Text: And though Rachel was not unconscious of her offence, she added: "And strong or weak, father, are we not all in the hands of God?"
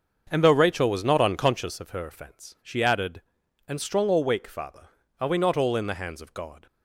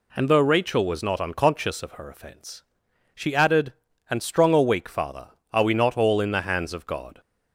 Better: second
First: starts louder than the rest; until 1.8 s; 6.5 dB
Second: none

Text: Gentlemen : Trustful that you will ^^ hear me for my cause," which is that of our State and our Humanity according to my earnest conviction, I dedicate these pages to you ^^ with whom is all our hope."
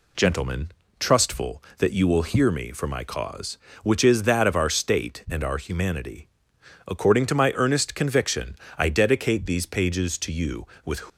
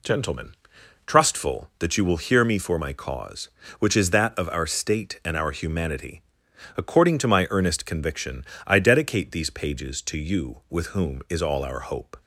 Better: second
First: pauses between "Humanity" and "according"; noticeable; at 6.2 s; 0.60 s long // stops before "whom is all our hope"; at 11.0 s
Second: pauses between "Humanity" and "according"; noticeable; at 6.2 s; 0.54 s long

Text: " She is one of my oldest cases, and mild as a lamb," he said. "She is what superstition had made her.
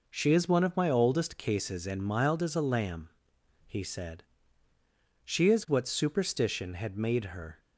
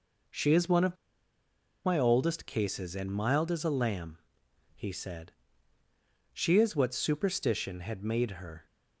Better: first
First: none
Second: pauses between "of" and "my"; noticeable; at 0.9 s; 0.89 s long

